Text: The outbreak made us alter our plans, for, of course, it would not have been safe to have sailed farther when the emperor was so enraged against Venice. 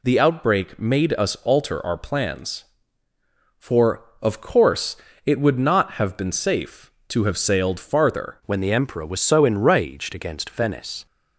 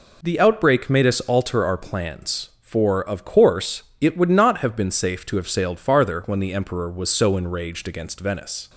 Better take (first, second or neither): second